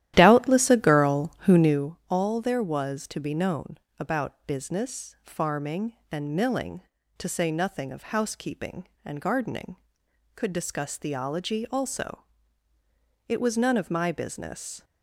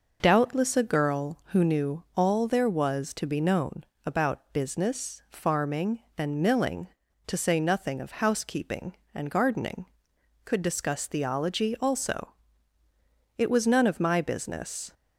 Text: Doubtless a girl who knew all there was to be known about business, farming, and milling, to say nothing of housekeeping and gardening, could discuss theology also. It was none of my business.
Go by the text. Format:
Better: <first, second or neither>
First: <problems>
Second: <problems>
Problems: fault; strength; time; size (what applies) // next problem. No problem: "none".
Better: second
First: starts louder than the rest; strong; until 1.9 s; 13 dB // pauses between "known" and "about"; slight; at 3.7 s; 0.22 s long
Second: pauses between "known" and "about"; slight; at 3.8 s; 0.22 s long